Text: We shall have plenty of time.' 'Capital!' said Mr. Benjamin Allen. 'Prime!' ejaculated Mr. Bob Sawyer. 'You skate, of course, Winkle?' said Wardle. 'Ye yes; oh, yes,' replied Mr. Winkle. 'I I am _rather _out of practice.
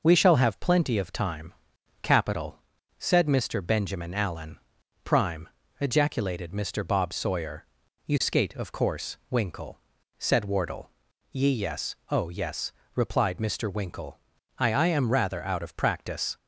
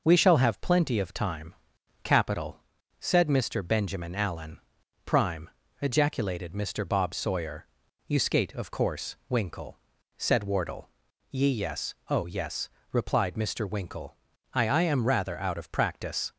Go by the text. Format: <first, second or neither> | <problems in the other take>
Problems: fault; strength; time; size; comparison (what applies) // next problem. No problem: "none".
neither | none